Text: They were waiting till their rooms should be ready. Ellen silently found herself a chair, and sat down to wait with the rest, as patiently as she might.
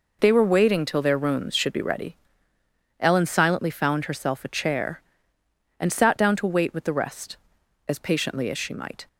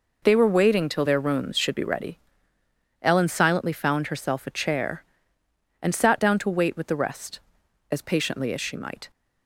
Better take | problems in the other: neither | none

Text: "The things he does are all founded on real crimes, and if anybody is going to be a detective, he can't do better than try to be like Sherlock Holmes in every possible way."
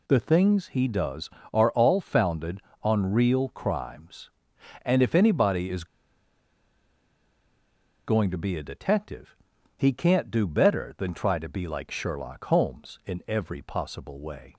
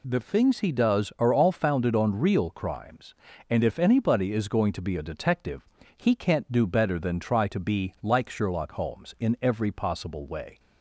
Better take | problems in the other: second | pauses between "is" and "going"; strong; at 5.8 s; 2.2 s long

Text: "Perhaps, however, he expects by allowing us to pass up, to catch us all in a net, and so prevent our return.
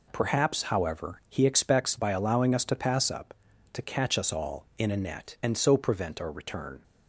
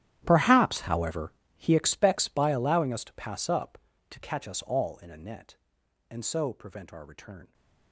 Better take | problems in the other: first | gets quieter; strong; throughout; 20.5 dB

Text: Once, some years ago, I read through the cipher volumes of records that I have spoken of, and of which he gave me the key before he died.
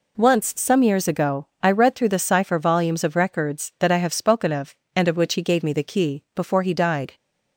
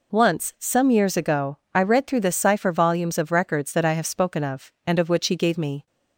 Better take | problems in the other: first | stops before "the key before he died"; at 5.8 s

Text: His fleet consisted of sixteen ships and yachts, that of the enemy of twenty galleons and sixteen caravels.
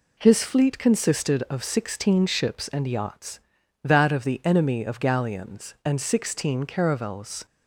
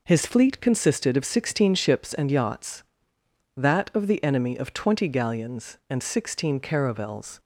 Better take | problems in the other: second | skips "twenty"; at 4.9 s

